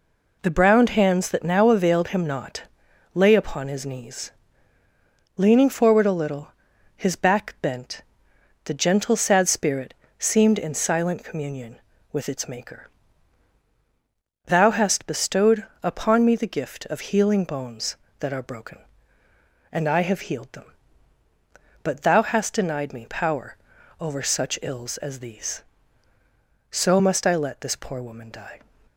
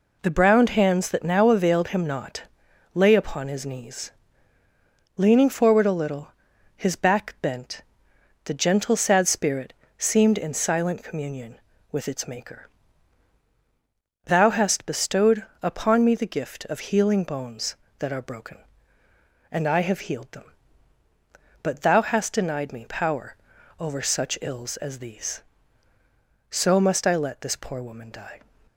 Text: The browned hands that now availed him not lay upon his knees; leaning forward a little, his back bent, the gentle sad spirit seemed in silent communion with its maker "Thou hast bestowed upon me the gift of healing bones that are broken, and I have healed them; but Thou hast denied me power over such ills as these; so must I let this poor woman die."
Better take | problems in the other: neither | pauses between "not" and "lay"; noticeable; the same in both // pauses between "spirit" and "seemed"; slight; the same in both // pauses between "maker" and "Thou"; strong; the same in both // pauses between "bestowed" and "upon"; slight; the same in both // pauses between "power" and "over"; the same in both

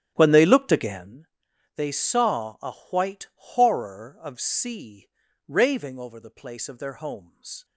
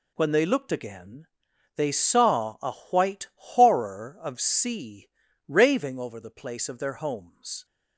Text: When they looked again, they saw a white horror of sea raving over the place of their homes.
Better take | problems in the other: second | starts louder than the rest; strong; until 1.1 s; 10.5 dB // pauses between "a" and "white"; slight; at 2.7 s; 0.18 s long; slight in the second // pauses between "sea" and "raving"; at 5.0 s; 0.40 s long; also in the second

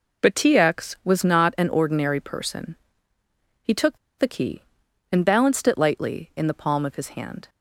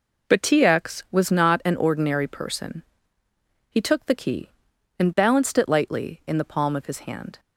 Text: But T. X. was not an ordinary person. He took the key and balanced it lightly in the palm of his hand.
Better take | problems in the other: second | pauses between "took" and "the"; slight; at 3.9 s; 0.20 s long

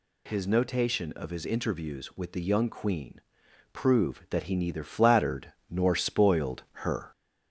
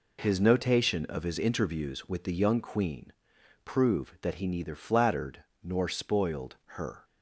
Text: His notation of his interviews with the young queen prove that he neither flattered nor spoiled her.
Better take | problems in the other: second | gets louder; slight; throughout; 2.5 dB // pauses between "queen" and "prove"; noticeable; at 3.2 s; 0.52 s long; noticeable in the second // pauses between "flattered" and "nor"; slight; at 5.5 s; 0.16 s long; slight in the second // pauses between "spoiled" and "her"; slight; at 6.6 s; 0.18 s long; slight in the second

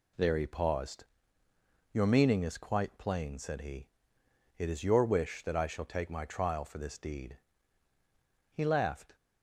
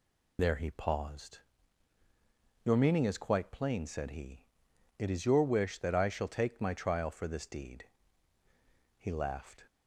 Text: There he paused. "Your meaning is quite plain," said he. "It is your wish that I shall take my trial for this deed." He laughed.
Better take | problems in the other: first | loses the start of "There"; at 0.3 s; 50 ms

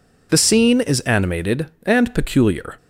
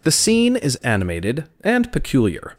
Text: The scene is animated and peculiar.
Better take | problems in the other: neither | none

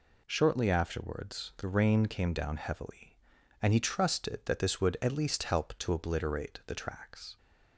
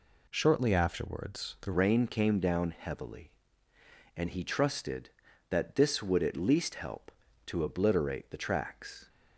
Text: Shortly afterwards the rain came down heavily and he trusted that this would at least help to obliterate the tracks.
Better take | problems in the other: first | changes voice at "rain"; from 1.7 s on; 7.3 s long

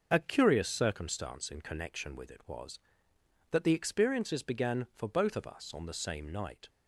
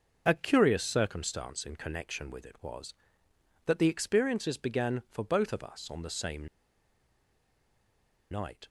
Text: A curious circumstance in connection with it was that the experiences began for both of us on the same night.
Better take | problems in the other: first | pauses between "same" and "night"; strong; at 6.4 s; 1.8 s long

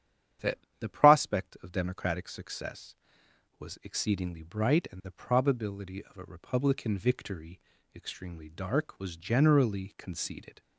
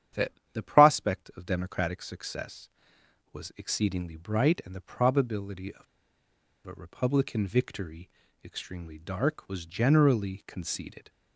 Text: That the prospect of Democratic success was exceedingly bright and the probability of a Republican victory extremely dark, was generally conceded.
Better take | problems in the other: first | starts louder than the rest; strong; until 1.4 s; 9.5 dB; strong in the first // pauses between "That" and "the"; slight; at 0.3 s; 0.22 s long; slight in the first // pauses between "of" and "a"; noticeable; at 5.8 s; 0.82 s long // pauses between "victory" and "extremely"; slight; at 8.0 s; 0.36 s long; slight in the first

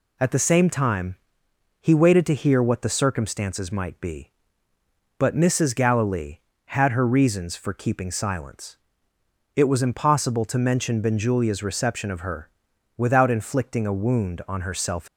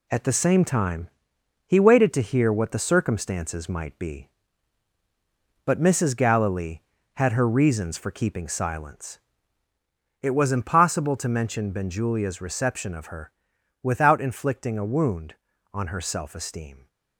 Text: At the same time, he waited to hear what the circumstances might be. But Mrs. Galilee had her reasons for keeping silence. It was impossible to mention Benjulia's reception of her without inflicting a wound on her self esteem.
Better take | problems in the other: second | pauses between "her" and "without"; noticeable; at 12.4 s; 0.46 s long; noticeable in the second // stops before "esteem"; at 15.0 s

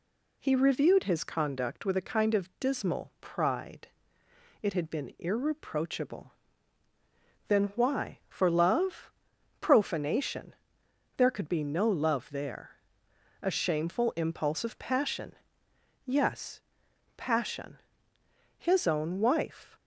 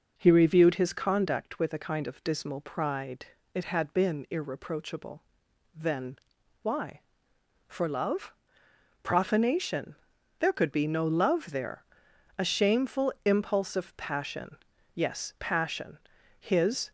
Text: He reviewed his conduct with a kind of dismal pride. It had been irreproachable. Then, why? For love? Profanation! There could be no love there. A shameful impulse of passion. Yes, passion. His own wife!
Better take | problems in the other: first | stops before "own wife"; at 16.8 s

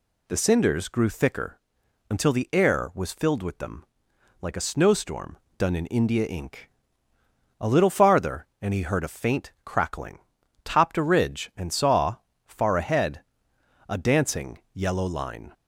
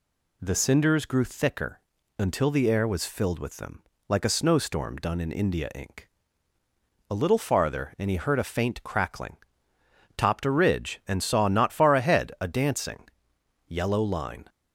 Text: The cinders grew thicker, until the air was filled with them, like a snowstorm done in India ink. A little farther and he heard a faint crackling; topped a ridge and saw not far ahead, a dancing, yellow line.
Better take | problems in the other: second | pauses between "snowstorm" and "done"; slight; at 5.3 s; 0.22 s long // skips "not"; at 12.3 s

